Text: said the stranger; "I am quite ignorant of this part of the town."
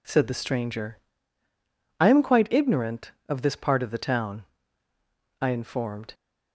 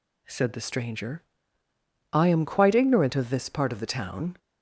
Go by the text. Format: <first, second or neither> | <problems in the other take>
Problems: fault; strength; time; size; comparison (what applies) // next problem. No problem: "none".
second | goes on to say "I informed"; noticeable; from 5.4 s on; 0.72 s long